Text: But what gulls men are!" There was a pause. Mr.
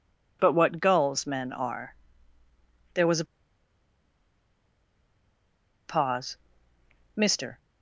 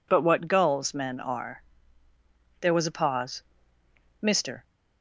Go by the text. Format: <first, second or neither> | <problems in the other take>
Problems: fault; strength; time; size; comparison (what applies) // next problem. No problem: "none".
second | pauses between "a" and "pause"; strong; at 3.2 s; 2.6 s long